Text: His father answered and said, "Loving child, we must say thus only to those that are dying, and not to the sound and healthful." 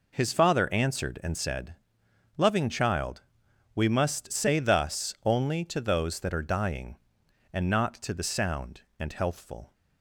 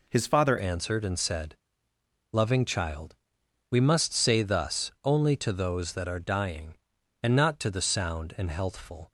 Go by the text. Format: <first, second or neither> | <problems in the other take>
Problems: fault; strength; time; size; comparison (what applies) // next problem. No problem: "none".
first | changes voice at "answered"; from 0.5 s on; 8.6 s long